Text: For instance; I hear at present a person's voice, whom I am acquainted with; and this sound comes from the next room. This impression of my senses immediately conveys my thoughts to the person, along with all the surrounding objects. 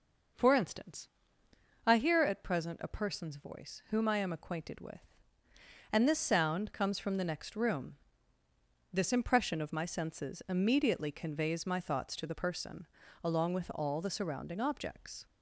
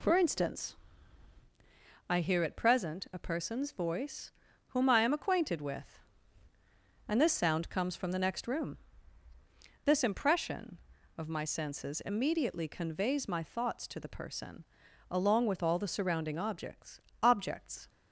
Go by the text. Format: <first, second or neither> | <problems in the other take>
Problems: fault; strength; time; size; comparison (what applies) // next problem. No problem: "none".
first | says "objects" twice; at 17.2 s